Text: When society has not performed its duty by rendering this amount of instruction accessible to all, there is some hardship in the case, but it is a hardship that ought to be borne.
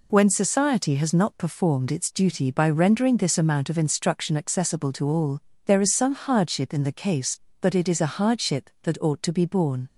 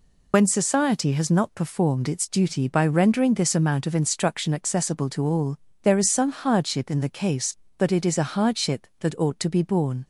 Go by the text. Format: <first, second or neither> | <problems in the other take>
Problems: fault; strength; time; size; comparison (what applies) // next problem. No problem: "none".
first | loses the start of "When"; at 0.3 s; 70 ms